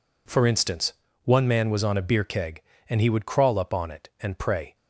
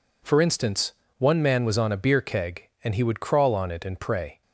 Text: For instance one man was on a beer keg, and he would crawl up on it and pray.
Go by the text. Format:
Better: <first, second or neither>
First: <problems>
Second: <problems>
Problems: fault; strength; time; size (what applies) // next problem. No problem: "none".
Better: first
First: pauses between "instance" and "one"; slight; at 0.9 s; 0.32 s long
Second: pauses between "instance" and "one"; slight; at 0.9 s; 0.26 s long // skips "up"; at 3.5 s